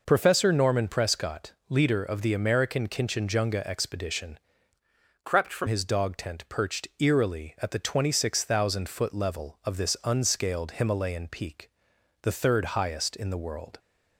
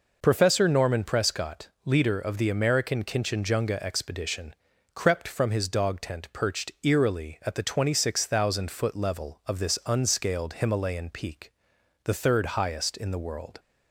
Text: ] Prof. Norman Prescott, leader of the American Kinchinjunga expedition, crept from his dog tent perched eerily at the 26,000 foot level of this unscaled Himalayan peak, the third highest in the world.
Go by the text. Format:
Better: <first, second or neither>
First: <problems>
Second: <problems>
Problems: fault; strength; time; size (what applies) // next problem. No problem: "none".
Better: second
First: changes voice from "crept" to "from"; from 5.2 to 5.6 s; 0.4 s long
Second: none